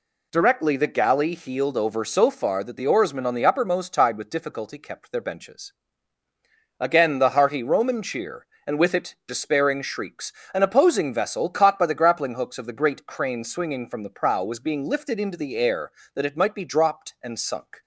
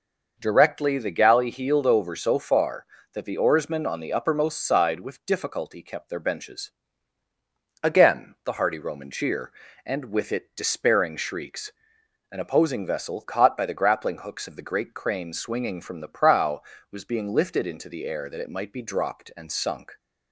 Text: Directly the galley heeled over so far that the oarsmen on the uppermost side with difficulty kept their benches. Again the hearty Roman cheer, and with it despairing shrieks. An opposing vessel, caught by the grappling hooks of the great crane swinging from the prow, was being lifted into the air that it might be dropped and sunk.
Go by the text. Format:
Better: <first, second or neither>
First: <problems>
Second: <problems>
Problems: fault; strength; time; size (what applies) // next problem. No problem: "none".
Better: second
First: says "tide" for "side"; at 3.9 s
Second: none